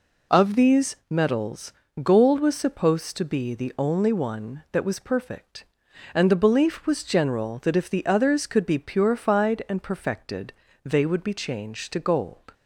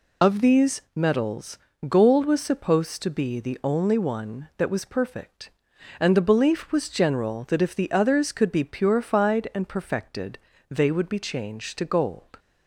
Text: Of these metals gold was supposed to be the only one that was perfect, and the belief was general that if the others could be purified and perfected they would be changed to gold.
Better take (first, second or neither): first